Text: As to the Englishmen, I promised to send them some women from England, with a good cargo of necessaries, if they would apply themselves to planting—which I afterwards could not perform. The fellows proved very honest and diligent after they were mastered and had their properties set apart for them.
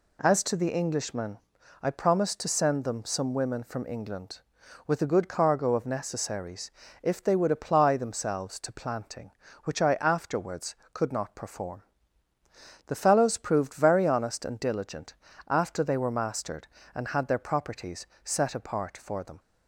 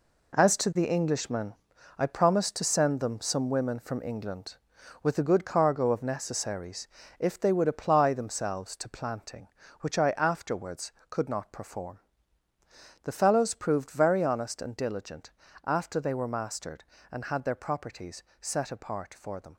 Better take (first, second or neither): first